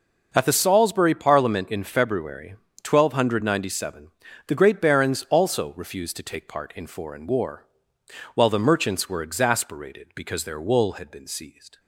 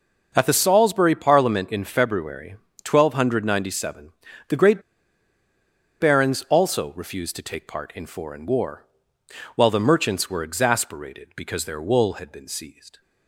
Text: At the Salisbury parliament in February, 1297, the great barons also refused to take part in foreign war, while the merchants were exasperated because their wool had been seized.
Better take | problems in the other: first | pauses between "great" and "barons"; at 4.8 s; 1.1 s long

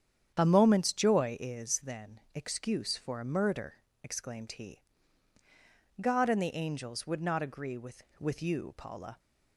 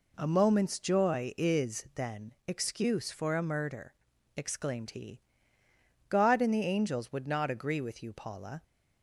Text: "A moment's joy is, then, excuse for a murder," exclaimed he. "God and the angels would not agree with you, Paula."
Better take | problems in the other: second | starts louder than the rest; strong; until 1.3 s; 9 dB // says "with" twice; at 8.1 s

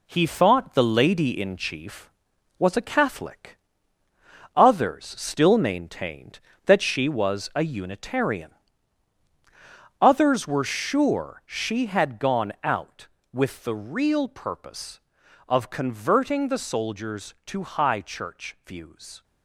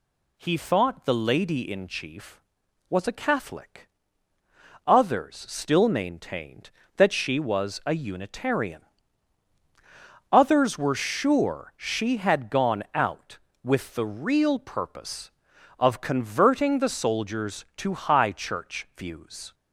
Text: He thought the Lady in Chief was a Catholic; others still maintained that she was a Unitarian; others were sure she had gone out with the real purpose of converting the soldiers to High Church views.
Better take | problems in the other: second | gets quieter; noticeable; throughout; 5.5 dB

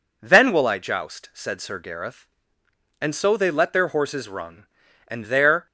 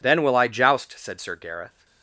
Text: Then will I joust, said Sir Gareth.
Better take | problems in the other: second | goes on to say "And so they let their horses run and there"; strong; from 3.0 s on; 2.6 s long

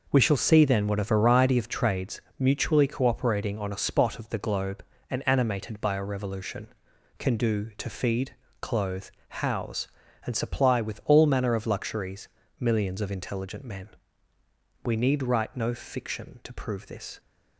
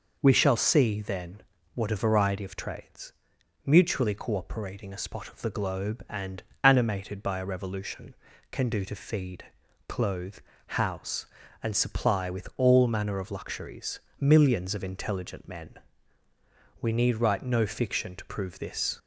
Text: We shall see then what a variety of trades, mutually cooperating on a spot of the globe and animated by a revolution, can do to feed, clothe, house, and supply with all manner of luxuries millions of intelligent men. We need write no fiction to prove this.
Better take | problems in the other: first | pauses between "then" and "what"; slight; at 1.4 s; 0.34 s long // skips "on"; at 4.9 s // pauses between "and" and "animated"; slight; at 6.4 s; 0.22 s long // pauses between "luxuries" and "millions"; slight; at 14.0 s; 0.18 s long; slight in the first

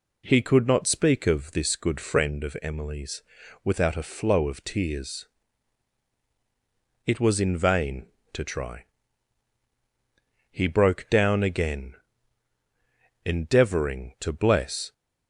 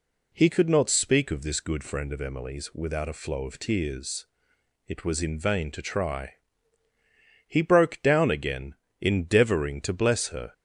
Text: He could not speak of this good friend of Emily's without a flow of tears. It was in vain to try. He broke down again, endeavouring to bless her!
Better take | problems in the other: second | pauses between "Emily's" and "without"; at 3.2 s; 0.42 s long // stops before "her"; at 14.9 s

